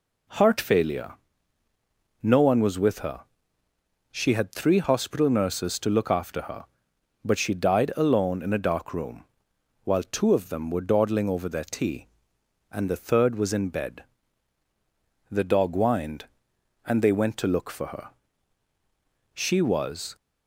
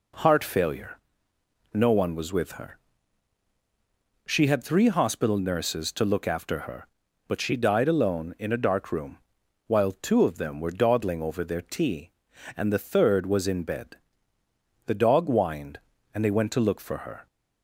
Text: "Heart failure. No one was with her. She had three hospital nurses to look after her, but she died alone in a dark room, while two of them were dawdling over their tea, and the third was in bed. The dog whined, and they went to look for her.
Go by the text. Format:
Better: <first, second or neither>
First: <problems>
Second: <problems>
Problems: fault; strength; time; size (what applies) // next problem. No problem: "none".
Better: second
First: goes on to say "She was"; noticeable; from 19.3 s on; 0.82 s long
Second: none